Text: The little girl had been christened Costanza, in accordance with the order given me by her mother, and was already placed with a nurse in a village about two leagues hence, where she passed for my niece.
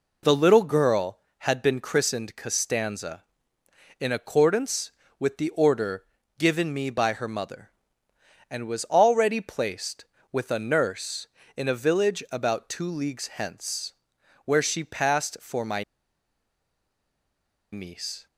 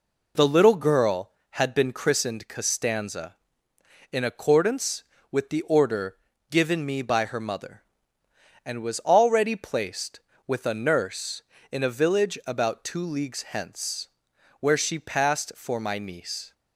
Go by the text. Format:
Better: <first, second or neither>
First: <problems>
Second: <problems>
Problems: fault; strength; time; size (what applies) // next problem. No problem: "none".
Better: second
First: pauses between "order" and "given"; slight; at 6.0 s; 0.34 s long // pauses between "my" and "niece"; strong; at 15.8 s; 1.8 s long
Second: pauses between "order" and "given"; slight; at 6.1 s; 0.34 s long